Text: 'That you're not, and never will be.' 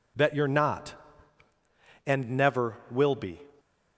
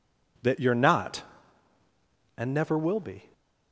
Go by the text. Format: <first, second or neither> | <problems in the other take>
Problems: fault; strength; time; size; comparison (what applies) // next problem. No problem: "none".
neither | none